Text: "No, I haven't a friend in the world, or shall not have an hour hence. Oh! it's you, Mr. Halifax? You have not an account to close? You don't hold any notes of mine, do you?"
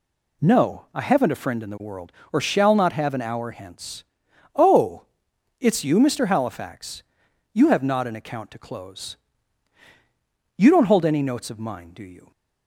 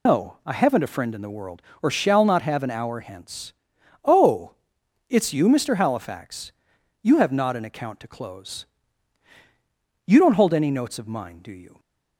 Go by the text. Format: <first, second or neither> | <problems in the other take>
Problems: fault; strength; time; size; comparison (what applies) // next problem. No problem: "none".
first | loses the start of "No"; at 0.0 s; 125 ms